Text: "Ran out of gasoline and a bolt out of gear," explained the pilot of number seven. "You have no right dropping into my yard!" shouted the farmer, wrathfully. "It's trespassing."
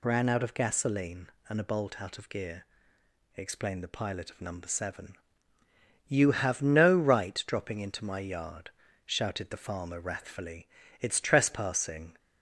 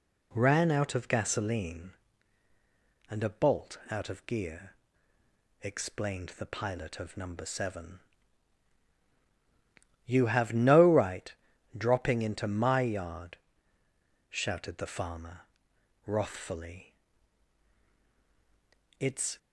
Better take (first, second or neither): first